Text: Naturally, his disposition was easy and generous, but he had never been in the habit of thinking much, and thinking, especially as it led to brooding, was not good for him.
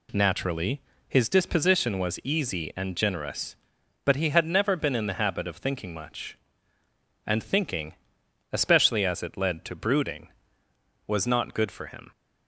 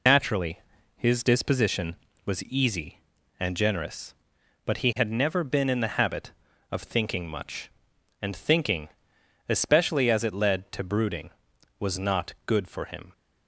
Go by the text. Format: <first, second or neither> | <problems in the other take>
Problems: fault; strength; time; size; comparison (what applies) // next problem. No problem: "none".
first | loses the start of "Naturally"; at 0.0 s; 85 ms